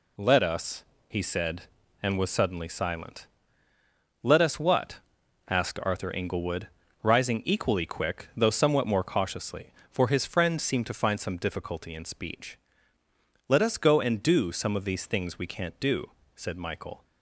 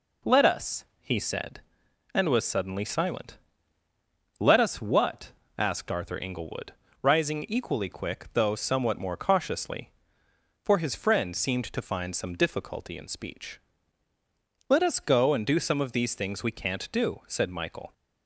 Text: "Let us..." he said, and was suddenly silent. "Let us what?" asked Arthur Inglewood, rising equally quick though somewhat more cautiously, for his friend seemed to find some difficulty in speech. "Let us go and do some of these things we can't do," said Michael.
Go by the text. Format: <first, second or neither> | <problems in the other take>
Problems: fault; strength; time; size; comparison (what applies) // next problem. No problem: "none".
neither | none